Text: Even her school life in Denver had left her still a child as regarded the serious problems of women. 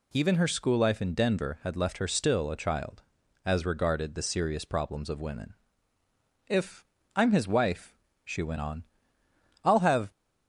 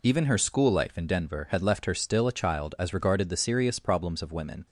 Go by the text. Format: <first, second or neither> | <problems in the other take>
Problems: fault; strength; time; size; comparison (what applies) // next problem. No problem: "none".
second | goes on to say "If I'm his wife she went on I'll have"; strong; from 6.4 s on; 3.6 s long